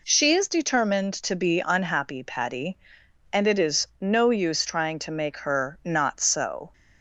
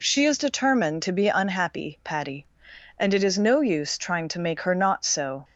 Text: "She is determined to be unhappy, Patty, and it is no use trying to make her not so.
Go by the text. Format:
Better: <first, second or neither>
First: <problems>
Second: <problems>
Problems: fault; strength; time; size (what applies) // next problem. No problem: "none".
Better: neither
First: none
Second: none